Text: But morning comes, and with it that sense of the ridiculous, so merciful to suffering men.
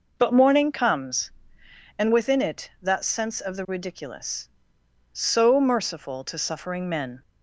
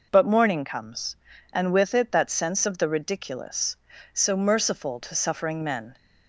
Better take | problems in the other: second | says "within" for "with"; at 2.1 s

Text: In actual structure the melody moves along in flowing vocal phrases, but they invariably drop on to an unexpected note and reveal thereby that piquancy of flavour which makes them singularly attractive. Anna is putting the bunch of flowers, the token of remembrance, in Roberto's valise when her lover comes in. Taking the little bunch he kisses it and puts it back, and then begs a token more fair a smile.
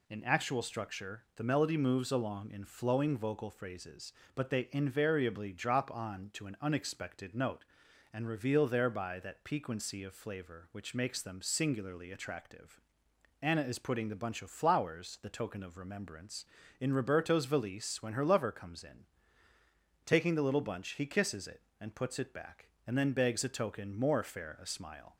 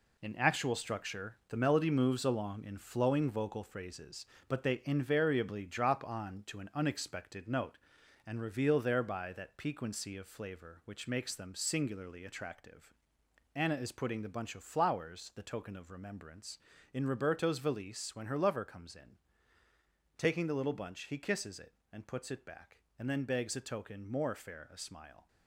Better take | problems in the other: first | gets quieter; strong; throughout; 7.5 dB

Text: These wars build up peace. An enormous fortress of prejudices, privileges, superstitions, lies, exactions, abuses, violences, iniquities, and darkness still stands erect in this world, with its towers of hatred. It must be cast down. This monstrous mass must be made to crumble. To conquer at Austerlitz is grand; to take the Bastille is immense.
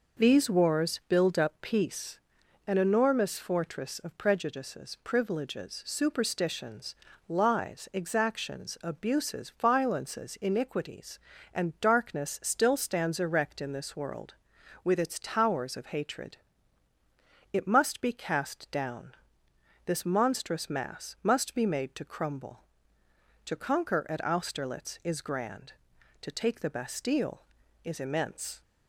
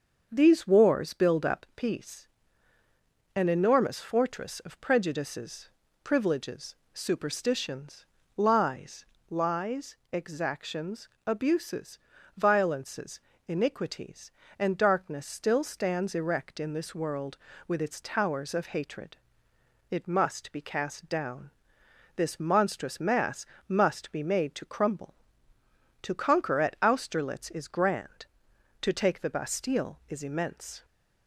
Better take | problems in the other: first | starts louder than the rest; until 1.3 s; 6.5 dB // says "lies" twice; at 9.3 s // pauses between "mass" and "must"; slight; at 23.4 s; 0.22 s long

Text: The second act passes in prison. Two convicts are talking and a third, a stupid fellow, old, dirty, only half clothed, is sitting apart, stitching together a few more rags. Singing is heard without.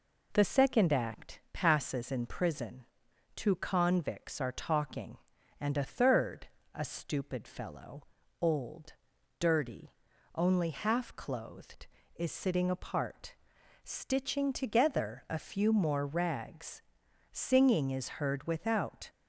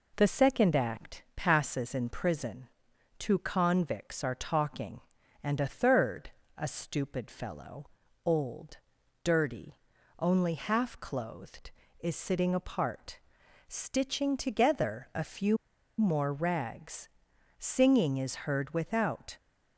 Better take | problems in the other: first | pauses between "few" and "more"; at 15.5 s; 0.43 s long

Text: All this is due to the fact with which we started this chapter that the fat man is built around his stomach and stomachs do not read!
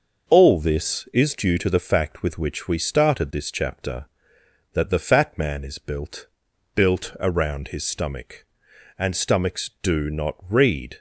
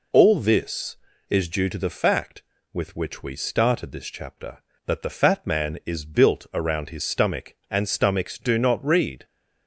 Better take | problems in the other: second | says "built" twice; at 6.7 s

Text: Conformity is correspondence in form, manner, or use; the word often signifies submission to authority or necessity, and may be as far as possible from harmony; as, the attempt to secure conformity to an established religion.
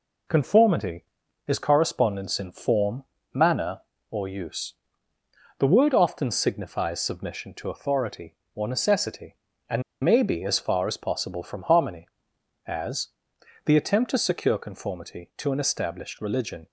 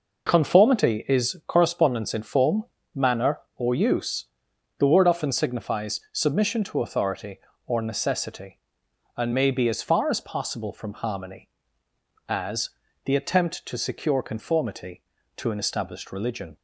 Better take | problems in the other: second | pauses between "and" and "may"; slight; at 9.8 s; 0.22 s long

